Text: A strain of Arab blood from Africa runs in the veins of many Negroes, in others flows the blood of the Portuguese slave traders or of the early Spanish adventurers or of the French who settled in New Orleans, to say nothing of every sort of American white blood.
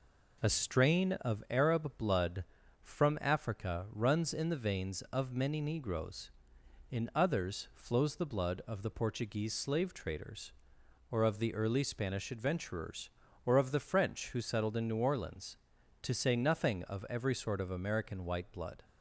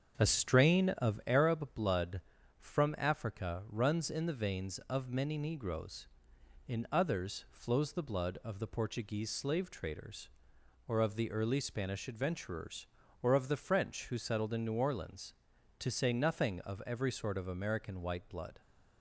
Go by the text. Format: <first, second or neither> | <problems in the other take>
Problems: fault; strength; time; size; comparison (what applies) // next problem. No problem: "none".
first | starts louder than the rest; until 1.5 s; 7 dB